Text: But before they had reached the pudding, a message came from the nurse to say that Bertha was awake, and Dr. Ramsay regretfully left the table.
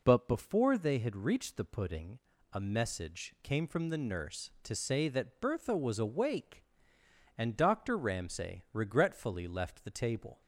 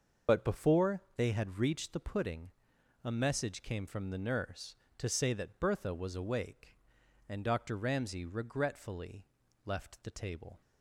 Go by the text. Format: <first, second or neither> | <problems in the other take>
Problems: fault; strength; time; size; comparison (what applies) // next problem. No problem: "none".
first | loses the start of "But"; at 0.2 s; 50 ms // starts louder than the rest; until 1.4 s; 6.5 dB // pauses between "regretfully" and "left"; at 9.2 s; 0.40 s long